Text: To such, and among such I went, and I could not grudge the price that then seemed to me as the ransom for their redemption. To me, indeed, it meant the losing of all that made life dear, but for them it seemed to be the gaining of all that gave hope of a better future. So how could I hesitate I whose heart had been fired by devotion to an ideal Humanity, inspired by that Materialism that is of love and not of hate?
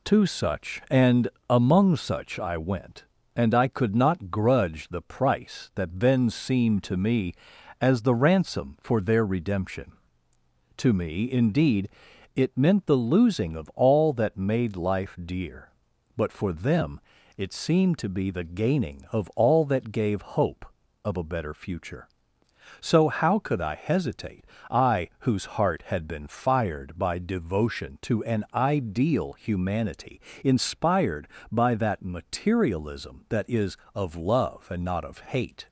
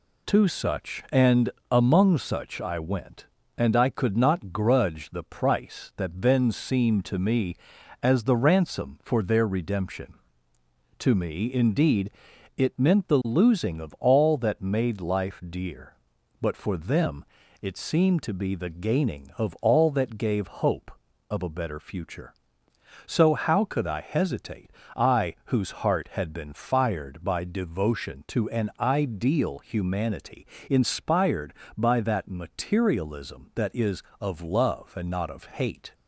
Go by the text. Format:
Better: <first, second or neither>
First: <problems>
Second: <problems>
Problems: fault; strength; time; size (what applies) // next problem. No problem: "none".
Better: neither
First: pauses between "and" and "among"; slight; at 1.2 s; 0.20 s long // pauses between "them" and "it"; at 16.9 s; 0.38 s long // pauses between "hesitate" and "I"; slight; at 24.4 s; 0.24 s long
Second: pauses between "and" and "among"; slight; at 1.5 s; 0.20 s long // pauses between "them" and "it"; at 17.2 s; 0.38 s long // pauses between "hesitate" and "I"; slight; at 24.7 s; 0.24 s long